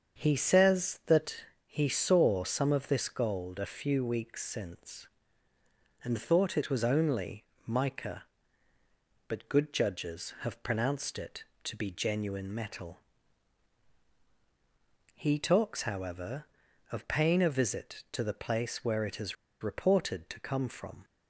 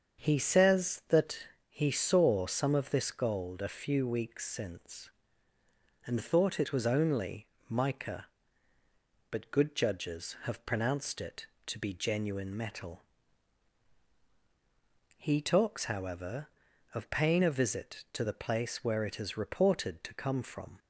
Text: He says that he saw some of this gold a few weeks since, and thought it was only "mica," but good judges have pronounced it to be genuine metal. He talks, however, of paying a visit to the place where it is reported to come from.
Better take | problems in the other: second | starts louder than the rest; until 1.2 s; 7 dB; also in the second // pauses between "that" and "he"; slight; at 1.3 s; 0.32 s long; slight in the second // pauses between "only" and "mica"; slight; at 7.4 s; 0.22 s long; slight in the second // pauses between "is" and "reported"; slight; at 19.3 s; 0.27 s long

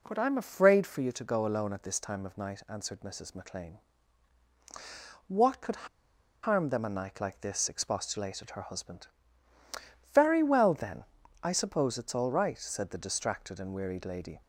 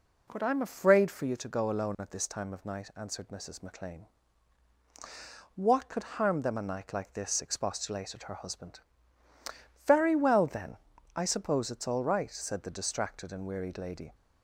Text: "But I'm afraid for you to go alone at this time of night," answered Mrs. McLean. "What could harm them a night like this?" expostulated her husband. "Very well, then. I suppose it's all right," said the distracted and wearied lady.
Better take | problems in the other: second | pauses between "could" and "harm"; noticeable; at 5.8 s; 0.55 s long

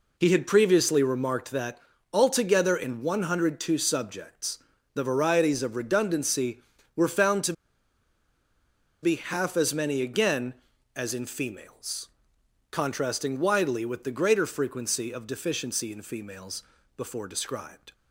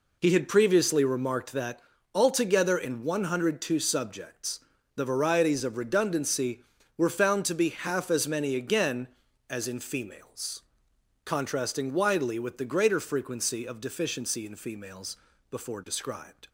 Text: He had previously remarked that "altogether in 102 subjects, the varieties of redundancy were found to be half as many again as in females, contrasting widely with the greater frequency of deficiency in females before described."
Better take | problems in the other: second | pauses between "that" and "altogether"; slight; at 1.7 s; 0.36 s long; slight in the second // pauses between "to" and "be"; strong; at 7.5 s; 1.4 s long // pauses between "females" and "before"; slight; at 16.6 s; 0.34 s long; slight in the second

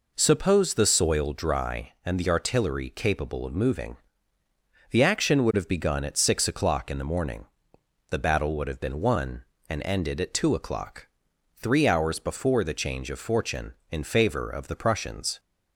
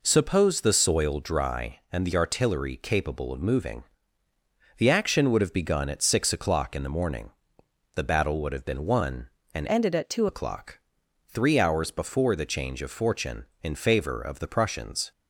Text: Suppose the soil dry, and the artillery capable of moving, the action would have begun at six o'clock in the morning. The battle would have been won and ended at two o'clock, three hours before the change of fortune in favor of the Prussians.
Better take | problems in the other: first | changes voice from "ended" to "two"; from 9.6 to 10.2 s; 0.6 s long

